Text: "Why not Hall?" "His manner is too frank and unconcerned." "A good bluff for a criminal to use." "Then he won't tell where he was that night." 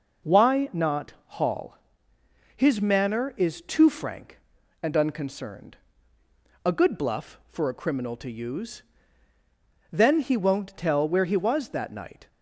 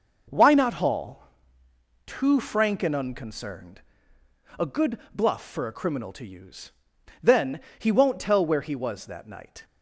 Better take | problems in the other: first | skips "His manner is"; at 1.6 s // pauses between "good" and "bluff"; slight; at 4.9 s; 0.16 s long // pauses between "Then" and "he"; slight; at 7.6 s; 0.18 s long

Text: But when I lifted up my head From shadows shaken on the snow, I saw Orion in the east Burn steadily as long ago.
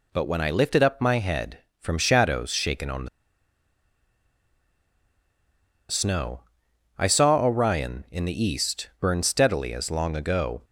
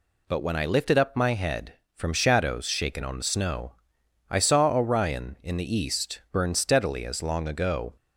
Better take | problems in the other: second | pauses between "the" and "snow"; strong; at 3.0 s; 2.8 s long

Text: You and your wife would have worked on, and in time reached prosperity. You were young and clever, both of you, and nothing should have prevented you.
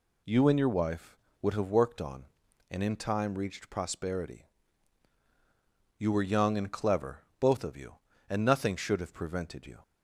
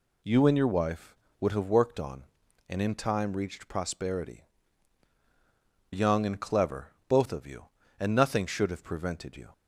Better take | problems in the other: first | skips "You were"; at 5.1 s

